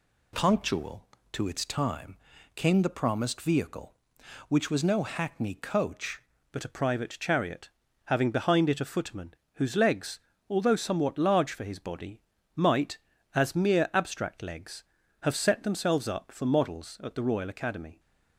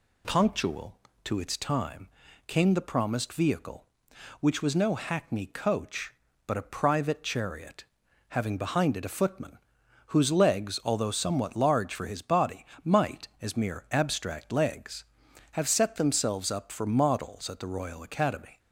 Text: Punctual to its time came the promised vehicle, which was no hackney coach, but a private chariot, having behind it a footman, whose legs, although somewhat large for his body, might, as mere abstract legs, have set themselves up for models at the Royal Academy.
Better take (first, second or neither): second